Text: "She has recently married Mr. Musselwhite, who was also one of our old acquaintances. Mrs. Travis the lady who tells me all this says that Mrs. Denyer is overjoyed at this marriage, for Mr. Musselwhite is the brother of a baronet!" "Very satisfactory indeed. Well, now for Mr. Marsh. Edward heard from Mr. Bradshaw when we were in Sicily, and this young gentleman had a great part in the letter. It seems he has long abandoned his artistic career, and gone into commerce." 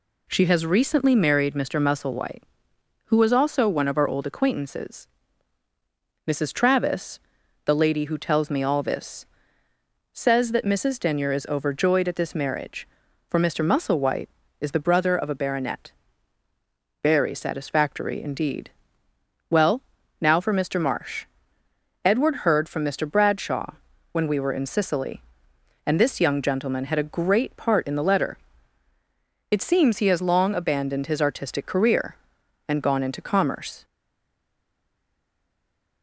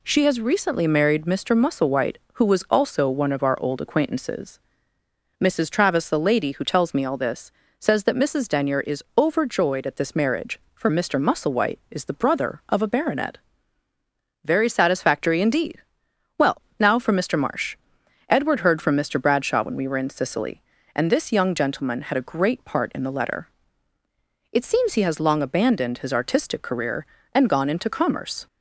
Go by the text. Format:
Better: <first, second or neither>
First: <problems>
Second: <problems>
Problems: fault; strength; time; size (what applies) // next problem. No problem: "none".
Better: second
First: pauses between "Travis" and "the"; noticeable; at 7.1 s; 0.46 s long // pauses between "this" and "says"; noticeable; at 9.2 s; 0.84 s long // pauses between "Bradshaw" and "when"; at 23.7 s; 0.38 s long // stays silent after the last word; from 33.8 s on; 2.2 s long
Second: pauses between "this" and "says"; slight; at 7.5 s; 0.28 s long